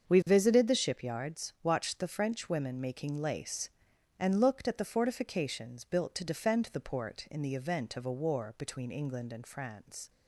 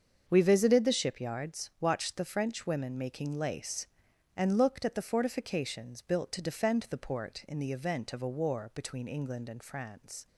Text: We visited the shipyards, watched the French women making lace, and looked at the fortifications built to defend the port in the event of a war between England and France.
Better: neither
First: starts louder than the rest; strong; until 1.1 s; 7 dB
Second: starts louder than the rest; until 1.2 s; 7 dB

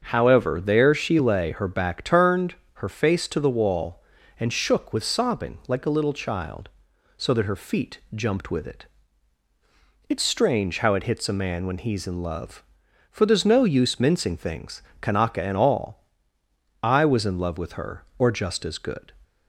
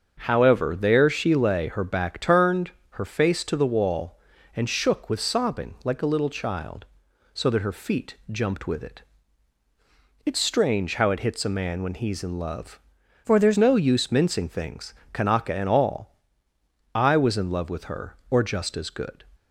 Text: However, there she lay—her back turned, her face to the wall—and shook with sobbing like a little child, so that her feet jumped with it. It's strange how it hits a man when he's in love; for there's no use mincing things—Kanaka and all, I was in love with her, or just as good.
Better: first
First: starts louder than the rest; until 1.0 s; 7 dB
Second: starts louder than the rest; until 1.2 s; 7 dB // changes voice from "for" to "there's"; from 13.2 to 13.5 s; 0.3 s long

